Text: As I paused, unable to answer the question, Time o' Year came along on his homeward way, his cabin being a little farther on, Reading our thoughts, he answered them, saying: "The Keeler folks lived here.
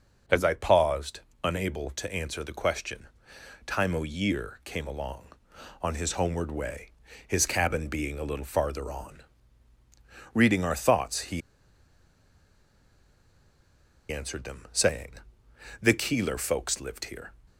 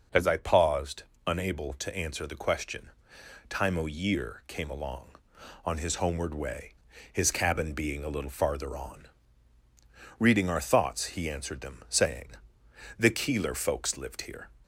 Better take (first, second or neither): second